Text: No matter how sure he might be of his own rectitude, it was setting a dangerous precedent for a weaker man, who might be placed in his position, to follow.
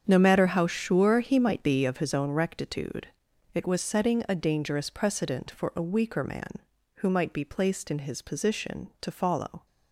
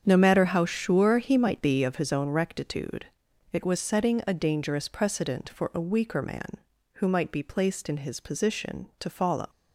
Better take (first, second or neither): first